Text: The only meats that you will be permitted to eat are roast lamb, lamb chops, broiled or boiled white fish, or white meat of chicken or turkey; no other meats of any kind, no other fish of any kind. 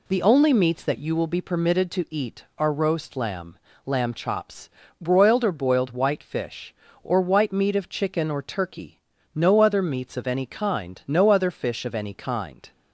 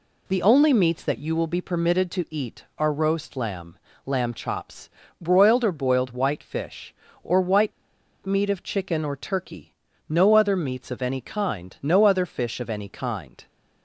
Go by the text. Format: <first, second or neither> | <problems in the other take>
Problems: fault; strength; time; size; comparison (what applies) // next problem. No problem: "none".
first | pauses between "white" and "meat"; noticeable; at 7.7 s; 0.54 s long